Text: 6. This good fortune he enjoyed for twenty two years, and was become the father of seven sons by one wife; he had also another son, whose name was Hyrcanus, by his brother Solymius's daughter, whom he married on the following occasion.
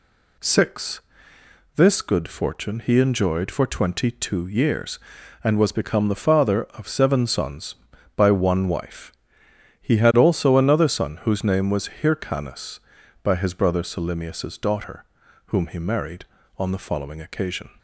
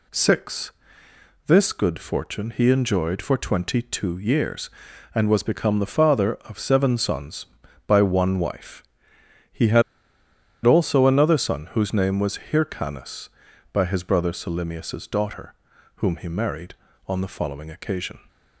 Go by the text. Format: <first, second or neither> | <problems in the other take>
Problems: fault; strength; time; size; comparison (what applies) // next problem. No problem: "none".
first | pauses between "had" and "also"; noticeable; at 9.8 s; 0.82 s long